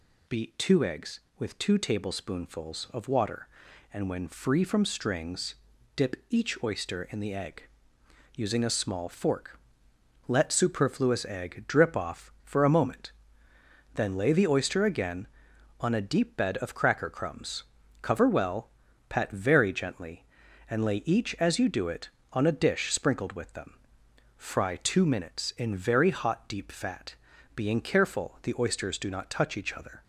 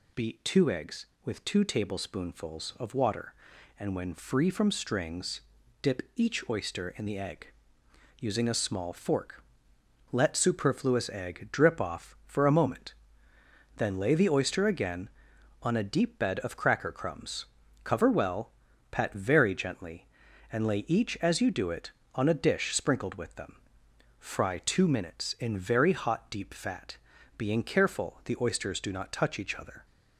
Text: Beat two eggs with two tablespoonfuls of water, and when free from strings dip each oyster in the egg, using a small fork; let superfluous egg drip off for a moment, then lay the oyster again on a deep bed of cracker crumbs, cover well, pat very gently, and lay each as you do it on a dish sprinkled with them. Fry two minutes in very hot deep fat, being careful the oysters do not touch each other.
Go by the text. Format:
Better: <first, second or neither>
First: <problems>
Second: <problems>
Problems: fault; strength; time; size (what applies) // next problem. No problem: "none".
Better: neither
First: pauses between "strings" and "dip"; at 5.5 s; 0.40 s long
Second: pauses between "strings" and "dip"; at 5.4 s; 0.40 s long